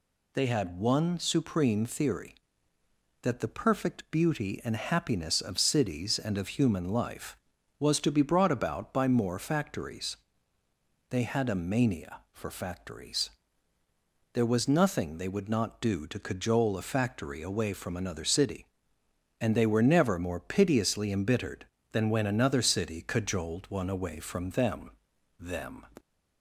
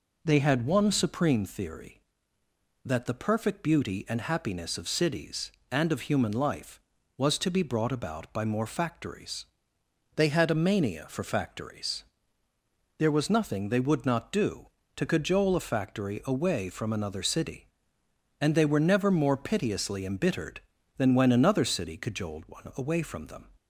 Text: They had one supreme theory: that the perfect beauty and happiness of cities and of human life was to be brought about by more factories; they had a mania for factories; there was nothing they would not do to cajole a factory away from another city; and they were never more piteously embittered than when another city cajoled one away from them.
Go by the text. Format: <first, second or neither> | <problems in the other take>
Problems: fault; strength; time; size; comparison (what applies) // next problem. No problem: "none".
second | says "them" twice; at 25.3 s